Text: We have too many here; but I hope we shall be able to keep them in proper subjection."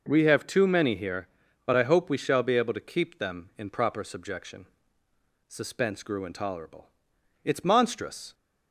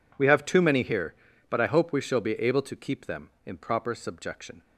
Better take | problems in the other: second | goes on to say "Suspense grew intolerable It's monstrous"; strong; from 5.4 s on; 2.8 s long

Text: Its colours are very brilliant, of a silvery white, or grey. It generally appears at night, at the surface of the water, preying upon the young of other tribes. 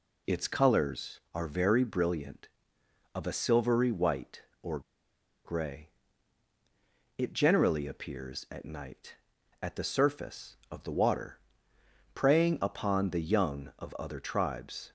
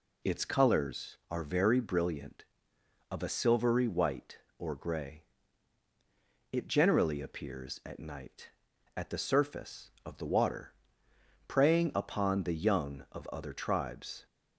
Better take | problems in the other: second | pauses between "or" and "grey"; noticeable; at 4.8 s; 0.64 s long

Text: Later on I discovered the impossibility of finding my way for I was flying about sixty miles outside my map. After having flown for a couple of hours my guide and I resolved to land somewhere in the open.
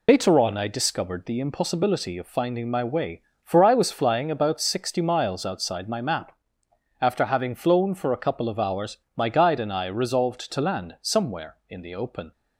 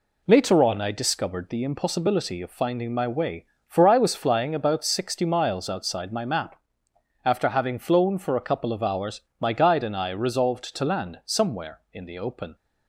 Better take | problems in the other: second | loses the start of "Later"; at 0.0 s; 75 ms // pauses between "hours" and "my"; slight; at 8.9 s; 0.20 s long; slight in the second

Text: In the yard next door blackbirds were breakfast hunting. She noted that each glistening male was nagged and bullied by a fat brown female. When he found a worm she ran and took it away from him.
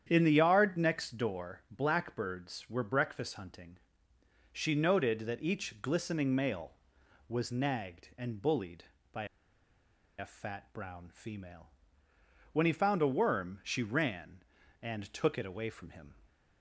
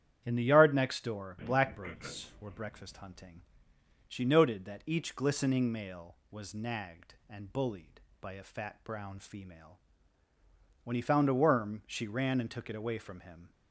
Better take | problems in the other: second | starts louder than the rest; strong; until 1.1 s; 9 dB; strong in the second // pauses between "by" and "a"; noticeable; at 9.2 s; 0.93 s long

